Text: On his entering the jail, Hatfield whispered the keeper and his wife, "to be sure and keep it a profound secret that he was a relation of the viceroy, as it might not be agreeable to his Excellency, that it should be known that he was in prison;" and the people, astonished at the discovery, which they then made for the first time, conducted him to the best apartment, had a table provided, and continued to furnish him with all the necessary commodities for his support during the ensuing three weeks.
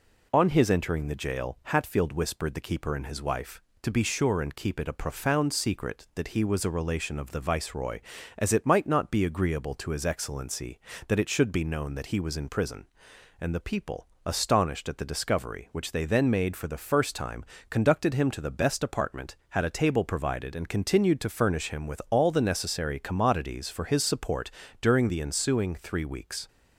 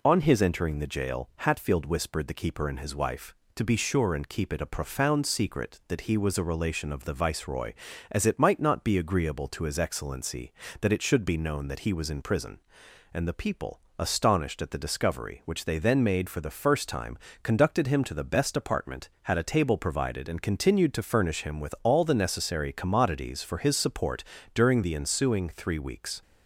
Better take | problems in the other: neither | pauses between "support" and "during"; slight; the same in both

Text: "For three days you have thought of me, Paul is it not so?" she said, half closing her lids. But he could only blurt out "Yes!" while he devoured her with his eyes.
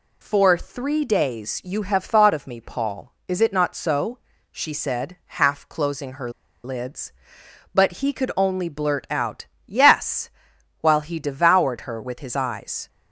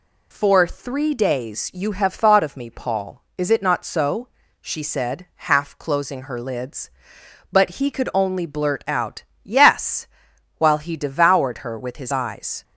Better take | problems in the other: second | pauses between "her" and "lids"; slight; at 6.3 s; 0.34 s long // pauses between "out" and "Yes"; slight; at 9.4 s; 0.18 s long; slight in the second

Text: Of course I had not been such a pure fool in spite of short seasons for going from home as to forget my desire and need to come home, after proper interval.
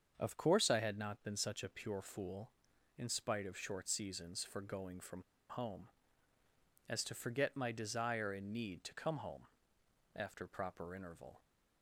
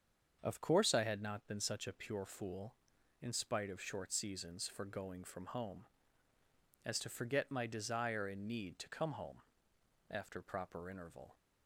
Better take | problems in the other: second | starts louder than the rest; until 1.1 s; 7 dB; also in the second // pauses between "from" and "home"; slight; at 5.2 s; 0.26 s long

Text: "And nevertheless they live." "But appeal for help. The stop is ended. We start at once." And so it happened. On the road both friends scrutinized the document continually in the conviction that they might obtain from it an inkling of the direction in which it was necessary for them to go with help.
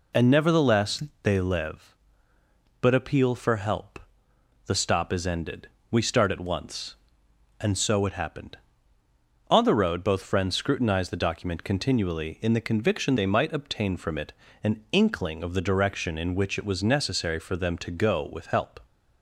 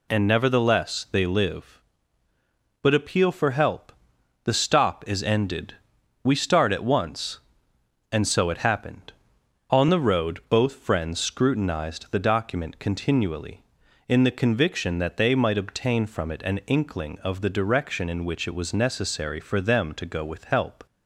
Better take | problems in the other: second | pauses between "nevertheless" and "they"; slight; at 1.0 s; 0.22 s long // skips "that"; at 13.1 s // pauses between "it" and "an"; slight; at 14.3 s; 0.30 s long

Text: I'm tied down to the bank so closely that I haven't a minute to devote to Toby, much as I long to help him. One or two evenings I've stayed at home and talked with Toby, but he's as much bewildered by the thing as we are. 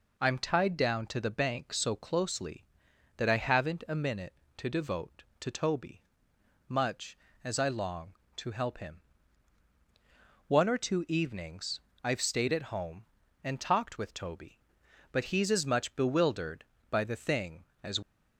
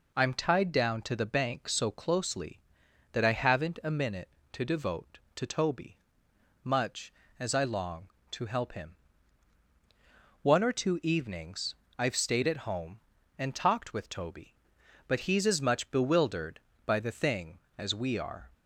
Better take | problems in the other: second | pauses between "evenings" and "I've"; slight; at 11.8 s; 0.22 s long; slight in the second // stops before "we are"; at 18.0 s

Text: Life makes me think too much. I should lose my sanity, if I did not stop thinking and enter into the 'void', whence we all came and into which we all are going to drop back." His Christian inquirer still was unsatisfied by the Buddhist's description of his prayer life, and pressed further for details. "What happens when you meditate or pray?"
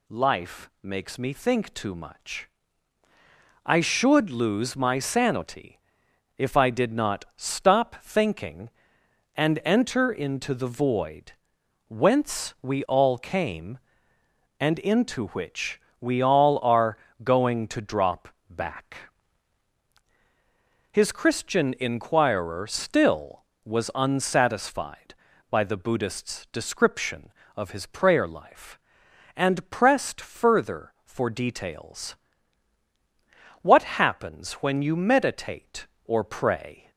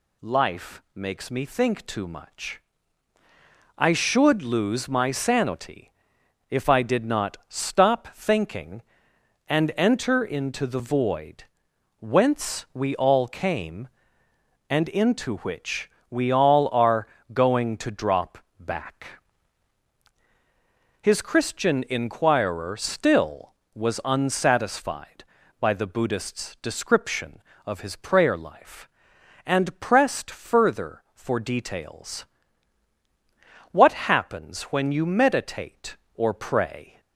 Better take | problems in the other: neither | pauses between "which" and "we"; slight; the same in both // pauses between "are" and "going"; slight; the same in both // pauses between "drop" and "back"; slight; the same in both

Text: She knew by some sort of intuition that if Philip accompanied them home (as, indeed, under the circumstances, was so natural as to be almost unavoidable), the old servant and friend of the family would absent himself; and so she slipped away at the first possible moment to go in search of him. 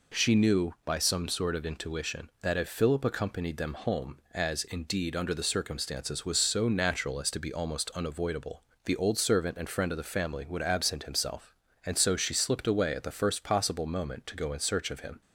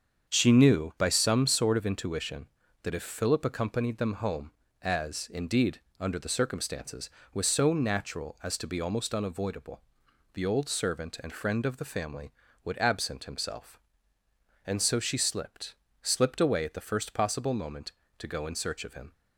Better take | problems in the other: first | starts louder than the rest; strong; until 1.3 s; 7 dB // says "slipped" twice; at 16.0 s

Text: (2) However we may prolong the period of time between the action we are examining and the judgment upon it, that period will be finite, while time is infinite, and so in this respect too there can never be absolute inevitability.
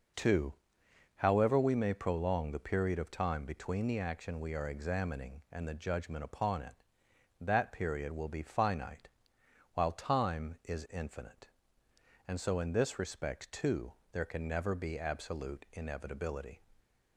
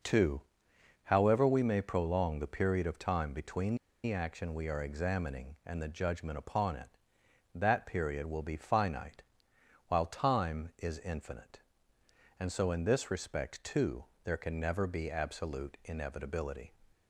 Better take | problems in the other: first | pauses between "between" and "the"; slight; at 3.7 s; 0.29 s long // pauses between "too" and "there"; slight; at 14.0 s; 0.18 s long; slight in the first

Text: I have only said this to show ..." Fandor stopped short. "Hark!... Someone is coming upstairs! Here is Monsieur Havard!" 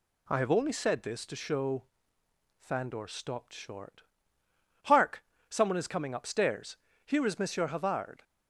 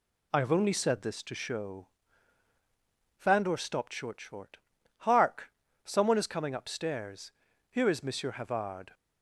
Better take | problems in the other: first | says "short" twice; at 4.2 s

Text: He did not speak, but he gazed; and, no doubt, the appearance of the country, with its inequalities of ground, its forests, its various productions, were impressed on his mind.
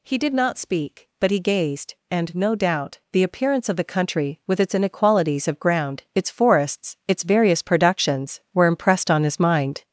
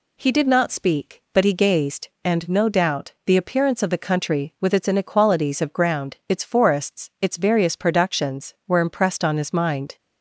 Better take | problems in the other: second | gets louder; noticeable; throughout; 4.5 dB

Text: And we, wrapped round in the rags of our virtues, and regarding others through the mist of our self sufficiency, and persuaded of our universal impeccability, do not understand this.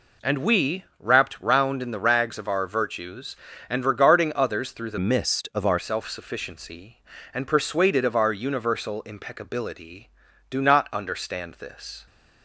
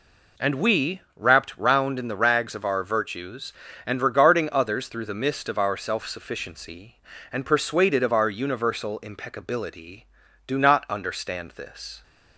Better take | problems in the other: second | changes voice from "mist" to "our"; from 4.9 to 5.7 s; 0.8 s long

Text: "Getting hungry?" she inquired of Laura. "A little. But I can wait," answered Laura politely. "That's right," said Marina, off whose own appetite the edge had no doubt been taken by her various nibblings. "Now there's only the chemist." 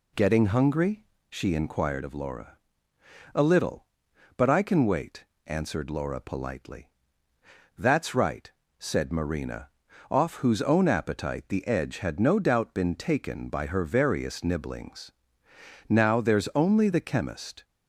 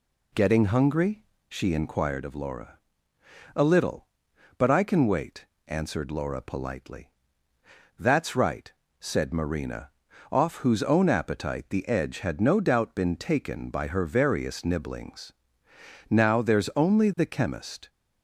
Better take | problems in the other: neither | none

